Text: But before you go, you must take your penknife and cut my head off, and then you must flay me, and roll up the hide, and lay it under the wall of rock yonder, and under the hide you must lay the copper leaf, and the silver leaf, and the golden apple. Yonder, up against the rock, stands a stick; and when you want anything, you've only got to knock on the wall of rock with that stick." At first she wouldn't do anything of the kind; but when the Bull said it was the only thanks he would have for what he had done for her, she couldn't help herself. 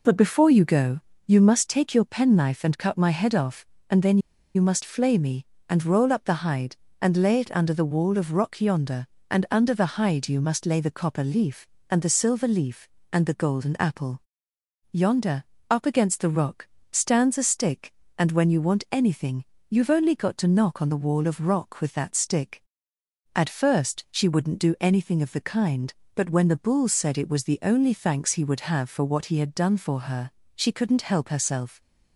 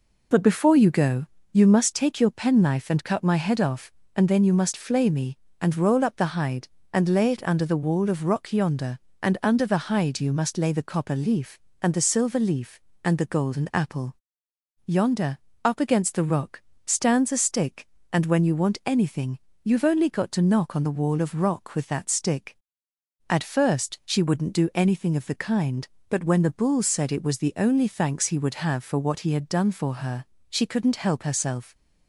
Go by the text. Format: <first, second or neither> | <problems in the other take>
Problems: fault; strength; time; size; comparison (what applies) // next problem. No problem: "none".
second | pauses between "then" and "you"; at 4.1 s; 0.36 s long